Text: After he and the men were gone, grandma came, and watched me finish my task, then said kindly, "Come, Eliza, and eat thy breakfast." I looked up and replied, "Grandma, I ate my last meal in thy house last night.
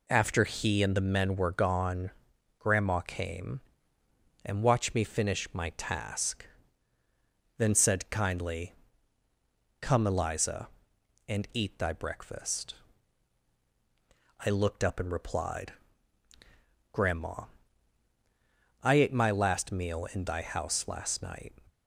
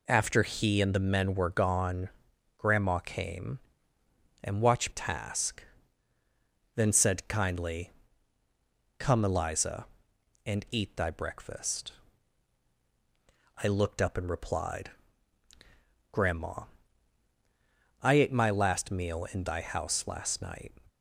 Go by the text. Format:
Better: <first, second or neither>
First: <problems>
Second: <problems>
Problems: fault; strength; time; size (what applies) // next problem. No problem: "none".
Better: first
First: none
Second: skips "me finish my"; at 4.9 s